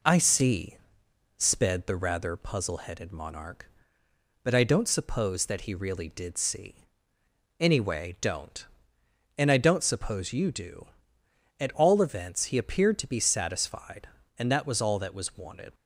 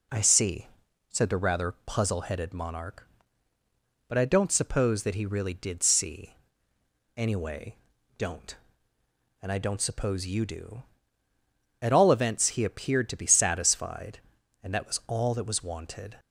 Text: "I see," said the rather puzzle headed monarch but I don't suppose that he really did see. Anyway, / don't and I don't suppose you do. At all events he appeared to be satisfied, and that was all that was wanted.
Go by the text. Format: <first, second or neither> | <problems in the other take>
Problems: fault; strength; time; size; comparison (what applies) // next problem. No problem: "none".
second | says "sped" for "said"; at 1.3 s